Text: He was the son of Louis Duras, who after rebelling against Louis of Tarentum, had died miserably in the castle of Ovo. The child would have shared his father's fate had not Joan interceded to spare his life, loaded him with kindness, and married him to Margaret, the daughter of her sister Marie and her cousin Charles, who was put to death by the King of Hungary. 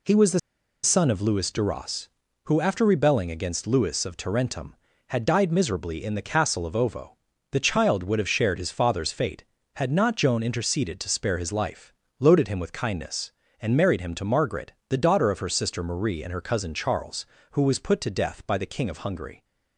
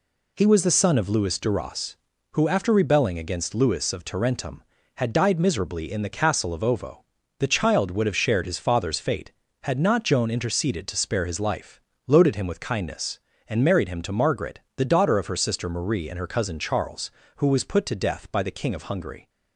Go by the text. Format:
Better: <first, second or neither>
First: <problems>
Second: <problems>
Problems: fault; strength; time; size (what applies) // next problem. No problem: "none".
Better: second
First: pauses between "the" and "son"; at 0.3 s; 0.44 s long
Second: none